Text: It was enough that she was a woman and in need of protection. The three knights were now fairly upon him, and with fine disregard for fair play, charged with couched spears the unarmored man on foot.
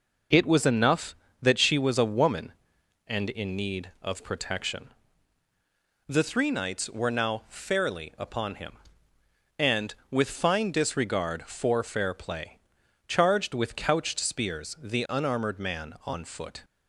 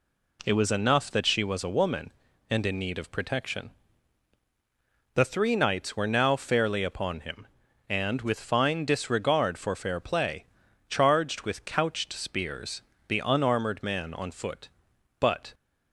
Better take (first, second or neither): first